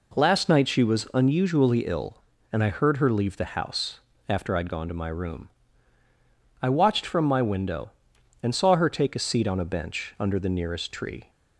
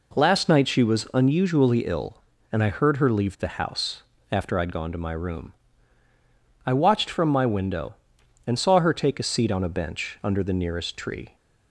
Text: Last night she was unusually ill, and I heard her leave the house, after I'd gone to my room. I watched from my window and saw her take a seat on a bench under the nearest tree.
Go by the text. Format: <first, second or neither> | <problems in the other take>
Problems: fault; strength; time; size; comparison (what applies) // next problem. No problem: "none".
neither | none